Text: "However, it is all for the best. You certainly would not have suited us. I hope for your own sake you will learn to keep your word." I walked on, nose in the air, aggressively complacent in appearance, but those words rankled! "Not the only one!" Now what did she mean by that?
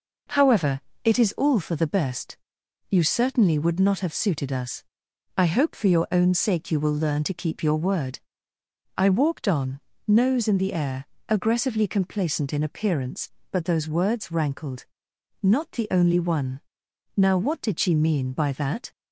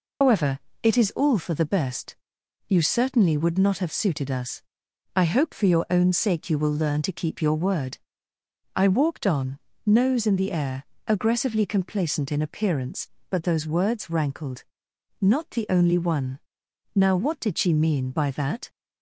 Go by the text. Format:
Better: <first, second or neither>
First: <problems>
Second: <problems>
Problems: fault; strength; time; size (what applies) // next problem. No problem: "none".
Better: first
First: none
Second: loses the start of "However"; at 0.2 s; 135 ms